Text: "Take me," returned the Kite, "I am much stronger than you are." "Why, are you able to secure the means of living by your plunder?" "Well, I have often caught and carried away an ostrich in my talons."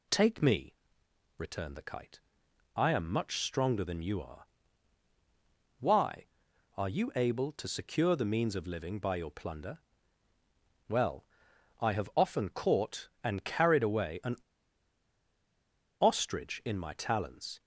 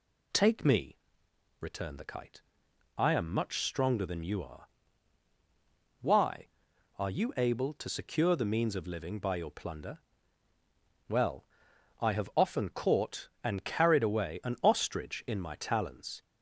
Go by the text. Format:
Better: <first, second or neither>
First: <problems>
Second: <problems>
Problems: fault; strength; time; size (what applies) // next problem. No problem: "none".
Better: second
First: pauses between "an" and "ostrich"; strong; at 14.3 s; 1.6 s long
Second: none